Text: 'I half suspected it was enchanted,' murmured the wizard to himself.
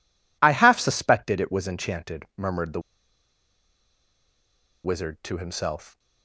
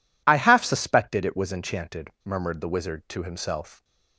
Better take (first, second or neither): second